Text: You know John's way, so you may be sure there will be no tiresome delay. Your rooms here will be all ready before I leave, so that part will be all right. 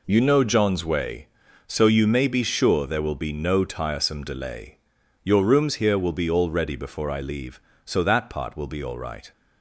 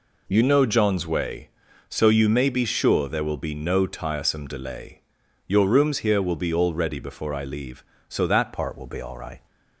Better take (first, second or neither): first